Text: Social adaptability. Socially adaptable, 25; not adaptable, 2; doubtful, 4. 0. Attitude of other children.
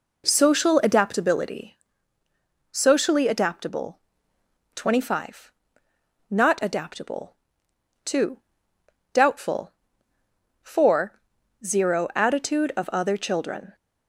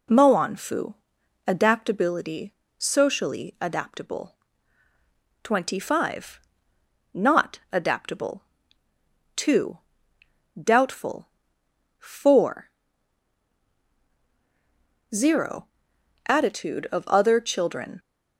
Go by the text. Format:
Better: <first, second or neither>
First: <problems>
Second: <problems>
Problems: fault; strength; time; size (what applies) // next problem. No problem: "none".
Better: first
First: none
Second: says "Moanfu" for "Social"; at 0.0 s